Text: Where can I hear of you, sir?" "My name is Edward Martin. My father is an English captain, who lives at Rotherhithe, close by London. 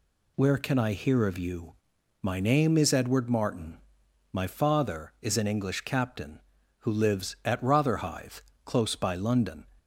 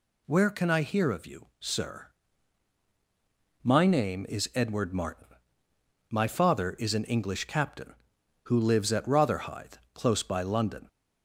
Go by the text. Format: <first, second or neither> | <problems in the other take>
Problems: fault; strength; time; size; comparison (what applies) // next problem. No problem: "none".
second | skips "sir"; at 1.9 s